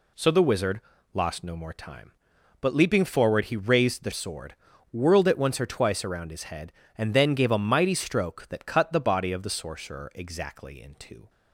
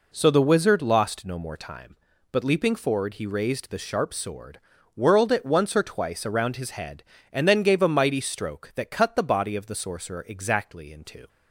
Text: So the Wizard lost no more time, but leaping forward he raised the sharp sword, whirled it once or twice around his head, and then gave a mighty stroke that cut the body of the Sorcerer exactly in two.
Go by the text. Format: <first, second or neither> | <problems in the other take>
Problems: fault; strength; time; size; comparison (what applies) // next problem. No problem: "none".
second | pauses between "Wizard" and "lost"; slight; at 0.7 s; 0.34 s long // skips "sharp"; at 4.1 s